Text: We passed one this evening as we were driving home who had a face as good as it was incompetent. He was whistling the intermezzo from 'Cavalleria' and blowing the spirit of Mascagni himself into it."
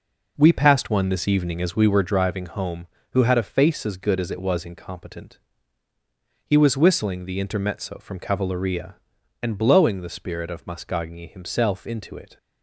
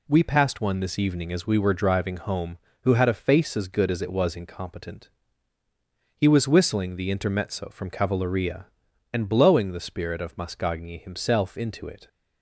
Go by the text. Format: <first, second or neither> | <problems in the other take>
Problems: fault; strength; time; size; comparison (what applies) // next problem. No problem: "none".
second | starts louder than the rest; noticeable; until 2.0 s; 5 dB